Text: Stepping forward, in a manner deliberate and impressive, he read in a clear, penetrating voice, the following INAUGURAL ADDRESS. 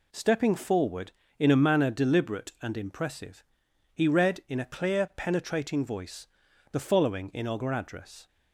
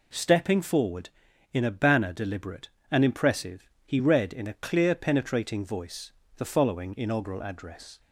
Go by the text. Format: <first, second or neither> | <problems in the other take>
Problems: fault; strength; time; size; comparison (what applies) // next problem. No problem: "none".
first | says "banner" for "manner"; at 1.6 s